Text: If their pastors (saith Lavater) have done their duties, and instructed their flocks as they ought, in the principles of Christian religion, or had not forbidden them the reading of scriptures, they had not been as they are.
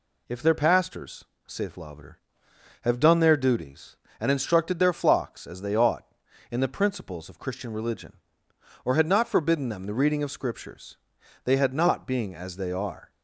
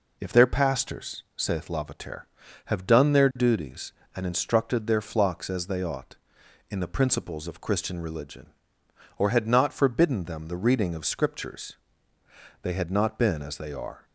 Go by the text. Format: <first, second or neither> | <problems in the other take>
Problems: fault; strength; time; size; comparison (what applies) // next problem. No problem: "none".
second | says "being" for "been"; at 12.0 s